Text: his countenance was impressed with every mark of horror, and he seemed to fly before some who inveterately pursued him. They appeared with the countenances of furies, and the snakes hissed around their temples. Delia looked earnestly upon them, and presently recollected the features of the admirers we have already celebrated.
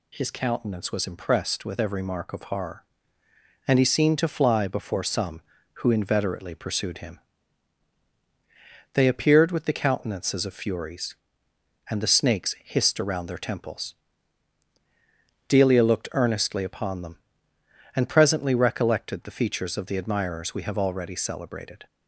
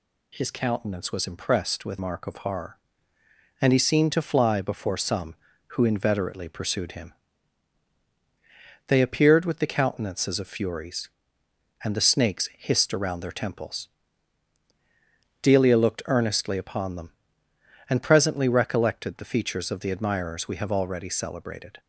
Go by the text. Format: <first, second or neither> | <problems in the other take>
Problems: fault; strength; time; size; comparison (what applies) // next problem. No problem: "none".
first | skips "every"; at 1.9 s